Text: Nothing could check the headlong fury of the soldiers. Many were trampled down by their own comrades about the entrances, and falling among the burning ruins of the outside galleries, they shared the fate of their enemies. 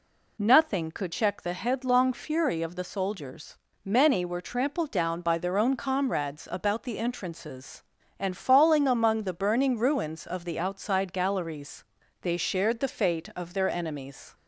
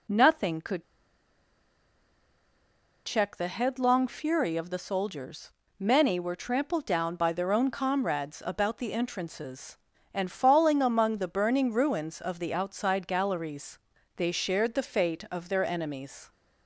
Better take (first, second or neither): first